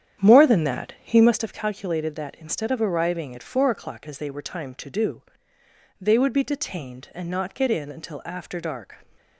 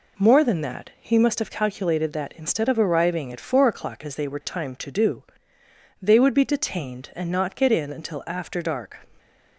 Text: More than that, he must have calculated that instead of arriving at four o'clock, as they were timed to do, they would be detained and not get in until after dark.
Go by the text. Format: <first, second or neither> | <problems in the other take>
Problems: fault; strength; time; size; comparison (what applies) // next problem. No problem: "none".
second | starts louder than the rest; strong; until 1.5 s; 9 dB